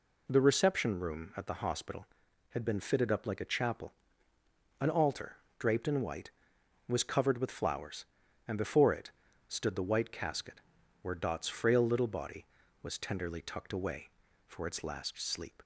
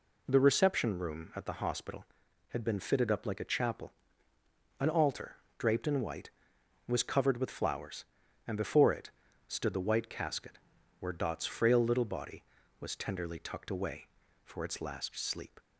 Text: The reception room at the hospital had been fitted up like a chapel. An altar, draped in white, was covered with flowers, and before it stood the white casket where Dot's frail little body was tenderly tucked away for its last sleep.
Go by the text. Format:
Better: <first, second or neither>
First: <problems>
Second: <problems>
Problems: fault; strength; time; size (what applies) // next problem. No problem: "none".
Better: neither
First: pauses between "it" and "stood"; at 9.1 s; 0.38 s long // pauses between "casket" and "where"; at 10.6 s; 0.40 s long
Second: pauses between "it" and "stood"; at 9.1 s; 0.38 s long // pauses between "casket" and "where"; at 10.5 s; 0.40 s long